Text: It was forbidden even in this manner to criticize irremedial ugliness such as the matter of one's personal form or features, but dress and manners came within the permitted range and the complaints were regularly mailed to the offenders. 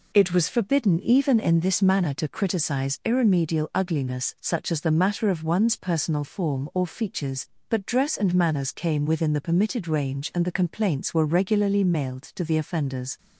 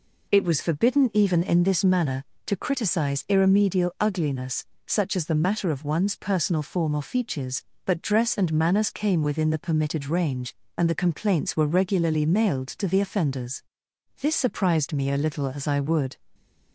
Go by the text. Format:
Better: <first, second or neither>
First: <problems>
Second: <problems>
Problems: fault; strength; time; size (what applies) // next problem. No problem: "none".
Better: first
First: none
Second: pauses between "ugliness" and "such"; slight; at 4.6 s; 0.24 s long // goes on to say "This surprised me a little as I would"; strong; from 14.2 s on; 1.9 s long